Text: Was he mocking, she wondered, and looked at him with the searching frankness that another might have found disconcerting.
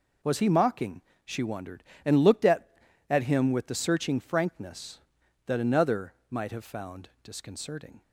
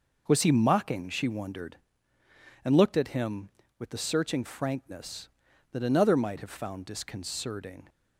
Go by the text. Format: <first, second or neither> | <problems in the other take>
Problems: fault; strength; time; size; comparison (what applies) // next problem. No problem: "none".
second | says "at" twice; at 3.0 s // pauses between "another" and "might"; slight; at 6.1 s; 0.16 s long